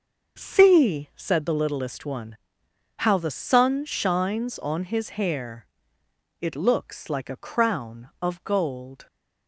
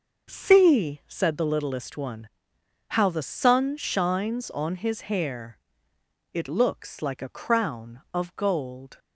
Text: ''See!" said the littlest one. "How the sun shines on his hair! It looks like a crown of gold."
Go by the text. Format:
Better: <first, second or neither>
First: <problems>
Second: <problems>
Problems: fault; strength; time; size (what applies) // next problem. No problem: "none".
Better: neither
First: none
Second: none